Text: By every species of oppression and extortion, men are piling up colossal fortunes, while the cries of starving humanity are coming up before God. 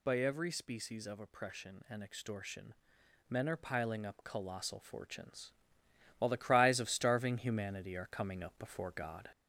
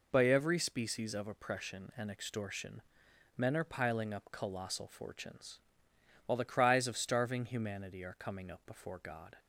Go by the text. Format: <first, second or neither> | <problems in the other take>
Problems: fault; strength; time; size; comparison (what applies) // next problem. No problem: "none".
second | gets louder; slight; throughout; 3 dB